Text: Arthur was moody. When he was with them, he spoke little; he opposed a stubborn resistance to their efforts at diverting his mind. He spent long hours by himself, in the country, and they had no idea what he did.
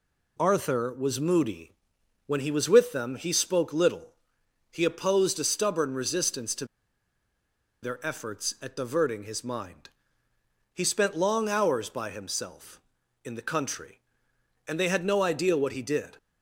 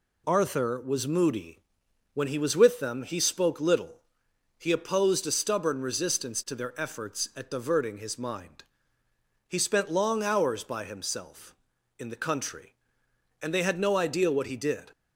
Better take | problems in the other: second | pauses between "to" and "their"; at 6.6 s; 1.1 s long

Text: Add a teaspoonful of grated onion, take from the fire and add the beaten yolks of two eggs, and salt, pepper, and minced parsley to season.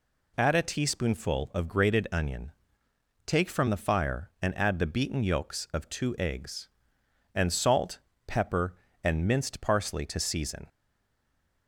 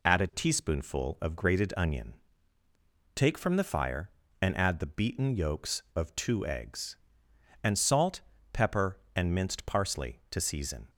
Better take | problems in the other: second | stays silent after the last word; slight; from 10.6 s on; 1.0 s long

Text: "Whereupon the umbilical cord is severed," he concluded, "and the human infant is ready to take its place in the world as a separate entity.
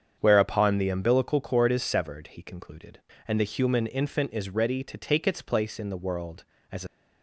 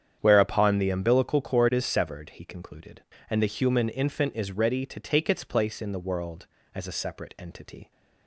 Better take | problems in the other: second | starts louder than the rest; strong; until 1.2 s; 7.5 dB; strong in the second // stops before "separate entity"; at 6.8 s

